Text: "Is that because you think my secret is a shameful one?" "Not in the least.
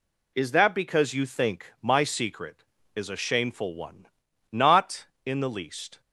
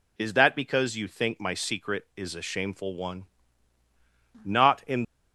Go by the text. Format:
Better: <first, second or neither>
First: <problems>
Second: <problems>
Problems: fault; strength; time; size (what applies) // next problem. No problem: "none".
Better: first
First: none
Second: stops before "the least"; at 5.0 s